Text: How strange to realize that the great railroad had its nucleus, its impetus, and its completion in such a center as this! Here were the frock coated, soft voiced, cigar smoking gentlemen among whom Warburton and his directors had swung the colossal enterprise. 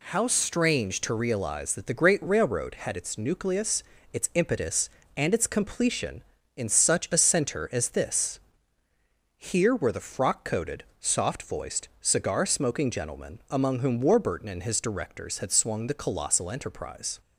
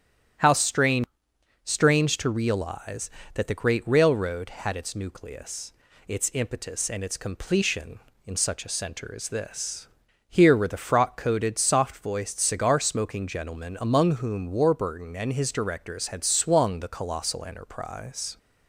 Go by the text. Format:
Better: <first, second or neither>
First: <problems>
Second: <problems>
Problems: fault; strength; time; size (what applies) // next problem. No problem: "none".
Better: first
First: none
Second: starts louder than the rest; strong; until 1.9 s; 10 dB // says "strange" twice; at 1.6 s